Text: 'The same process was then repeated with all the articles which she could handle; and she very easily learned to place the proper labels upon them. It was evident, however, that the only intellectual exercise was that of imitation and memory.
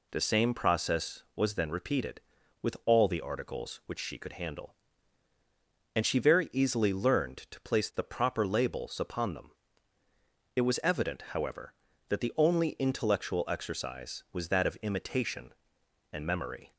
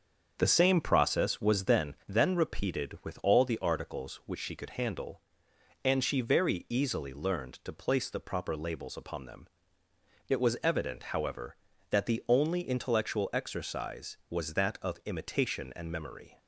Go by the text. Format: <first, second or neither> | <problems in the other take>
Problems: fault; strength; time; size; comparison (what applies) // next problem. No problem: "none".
first | starts louder than the rest; until 1.3 s; 7 dB // says "then" twice; at 2.0 s